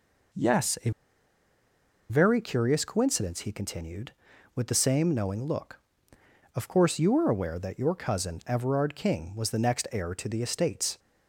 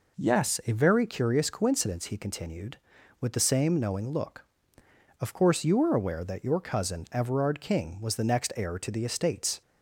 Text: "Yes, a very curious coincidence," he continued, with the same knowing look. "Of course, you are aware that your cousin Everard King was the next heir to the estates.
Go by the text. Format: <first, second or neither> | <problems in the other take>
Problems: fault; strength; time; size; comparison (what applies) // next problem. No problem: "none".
second | pauses between "a" and "very"; at 0.8 s; 1.1 s long